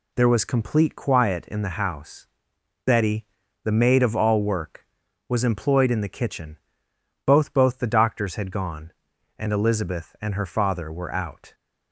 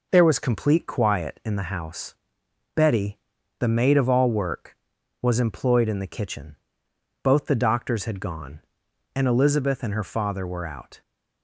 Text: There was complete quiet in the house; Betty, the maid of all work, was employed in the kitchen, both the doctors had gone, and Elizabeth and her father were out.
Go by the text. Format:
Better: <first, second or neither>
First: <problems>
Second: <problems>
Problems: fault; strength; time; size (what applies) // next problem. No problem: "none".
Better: second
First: says "both" twice; at 7.5 s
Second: none